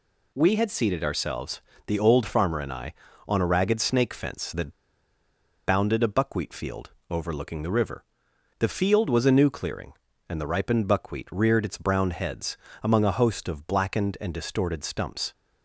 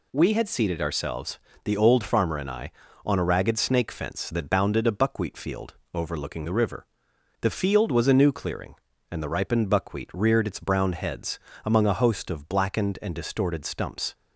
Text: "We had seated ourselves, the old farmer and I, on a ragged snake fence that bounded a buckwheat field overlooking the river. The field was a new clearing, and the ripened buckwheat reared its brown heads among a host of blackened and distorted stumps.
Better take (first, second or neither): second